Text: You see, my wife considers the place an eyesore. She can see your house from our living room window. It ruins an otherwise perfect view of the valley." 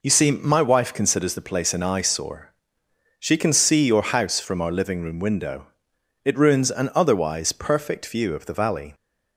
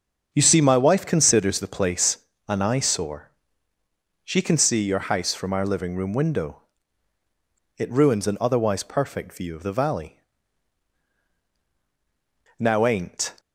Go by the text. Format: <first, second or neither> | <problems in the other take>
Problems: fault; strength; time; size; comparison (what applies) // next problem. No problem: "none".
first | starts louder than the rest; until 1.3 s; 7 dB // pauses between "place" and "an"; slight; at 2.1 s; 0.30 s long // goes on to say "Now ain't"; noticeable; from 12.5 s on; 0.74 s long